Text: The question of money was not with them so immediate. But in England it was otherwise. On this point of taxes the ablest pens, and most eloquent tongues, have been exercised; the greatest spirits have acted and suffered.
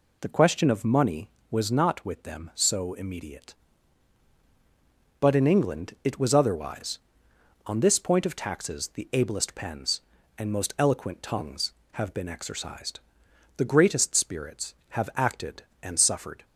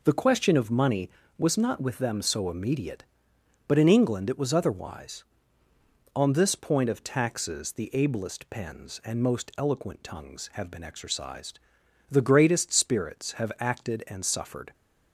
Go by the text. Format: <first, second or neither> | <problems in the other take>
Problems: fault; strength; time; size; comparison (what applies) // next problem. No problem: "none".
neither | none